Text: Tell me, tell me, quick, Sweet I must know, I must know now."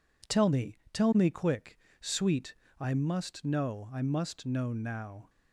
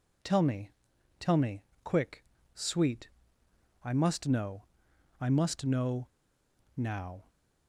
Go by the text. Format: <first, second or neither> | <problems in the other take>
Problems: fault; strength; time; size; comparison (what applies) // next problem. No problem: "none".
first | pauses between "Sweet" and "I"; noticeable; at 3.0 s; 0.74 s long; slight in the first // pauses between "know" and "now"; noticeable; at 6.0 s; 0.67 s long